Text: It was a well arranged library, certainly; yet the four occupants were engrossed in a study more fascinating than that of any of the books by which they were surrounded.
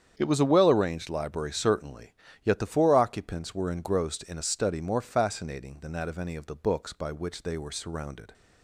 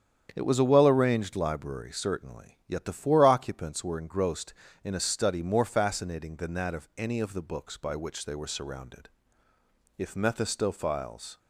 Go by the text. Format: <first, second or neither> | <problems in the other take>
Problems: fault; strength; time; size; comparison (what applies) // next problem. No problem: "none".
first | starts louder than the rest; strong; until 1.3 s; 8.5 dB; strong in the first // goes on to say "If Mephistophiles"; from 9.9 s on; 1.4 s long